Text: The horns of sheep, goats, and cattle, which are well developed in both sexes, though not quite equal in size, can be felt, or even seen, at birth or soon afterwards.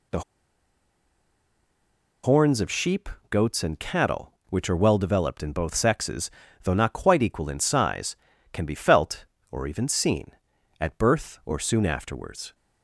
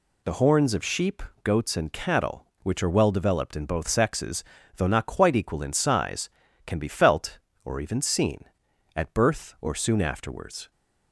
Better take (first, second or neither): second